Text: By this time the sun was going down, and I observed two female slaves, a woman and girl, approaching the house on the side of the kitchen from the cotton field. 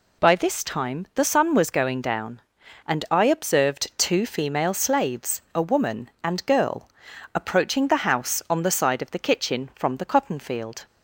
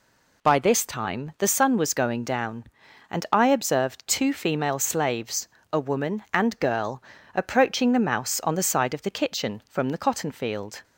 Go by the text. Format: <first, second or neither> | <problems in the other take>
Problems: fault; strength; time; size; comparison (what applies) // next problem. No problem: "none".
first | says "mouse" for "house"; at 7.9 s